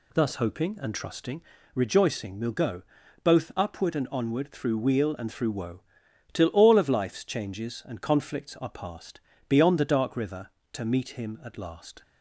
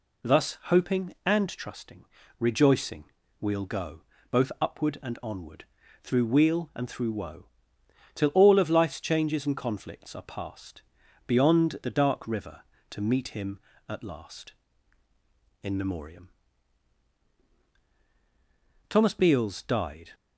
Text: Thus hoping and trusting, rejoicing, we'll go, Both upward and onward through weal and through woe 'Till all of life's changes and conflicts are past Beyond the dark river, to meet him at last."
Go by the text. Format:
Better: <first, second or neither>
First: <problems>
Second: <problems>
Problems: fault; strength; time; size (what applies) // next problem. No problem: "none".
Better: first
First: pauses between "woe" and "Till"; noticeable; at 5.8 s; 0.52 s long // pauses between "past" and "Beyond"; slight; at 9.1 s; 0.28 s long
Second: pauses between "onward" and "through"; at 5.6 s; 0.38 s long // pauses between "woe" and "Till"; noticeable; at 7.4 s; 0.66 s long // pauses between "past" and "Beyond"; at 10.8 s; 0.42 s long // goes on to say "In Memoriam Thomas Beals died"; strong; from 15.6 s on; 4.5 s long